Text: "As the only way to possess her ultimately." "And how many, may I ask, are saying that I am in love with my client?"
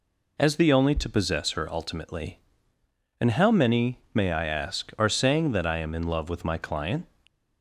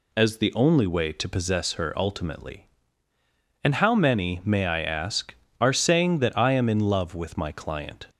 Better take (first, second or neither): second